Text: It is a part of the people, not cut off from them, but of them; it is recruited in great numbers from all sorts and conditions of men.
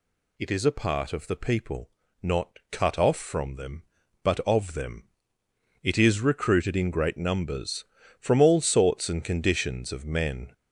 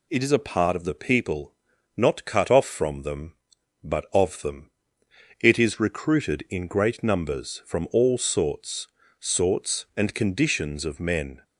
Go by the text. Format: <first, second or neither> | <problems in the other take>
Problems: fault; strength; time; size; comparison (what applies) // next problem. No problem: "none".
first | says "sorts" twice; at 9.1 s